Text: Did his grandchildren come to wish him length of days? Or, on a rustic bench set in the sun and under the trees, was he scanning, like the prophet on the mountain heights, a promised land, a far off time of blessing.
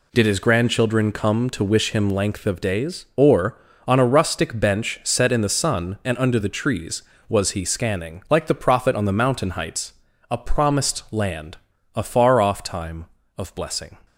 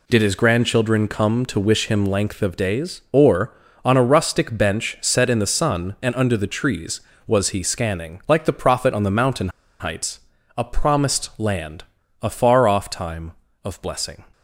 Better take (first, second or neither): first